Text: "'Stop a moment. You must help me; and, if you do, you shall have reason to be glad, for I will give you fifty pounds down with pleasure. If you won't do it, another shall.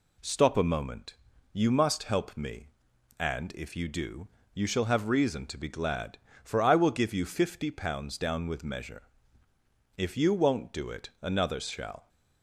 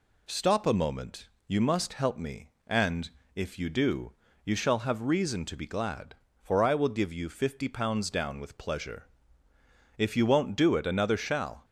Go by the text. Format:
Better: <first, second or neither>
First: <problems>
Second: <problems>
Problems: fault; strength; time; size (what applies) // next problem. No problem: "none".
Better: second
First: says "measure" for "pleasure"; at 8.6 s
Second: none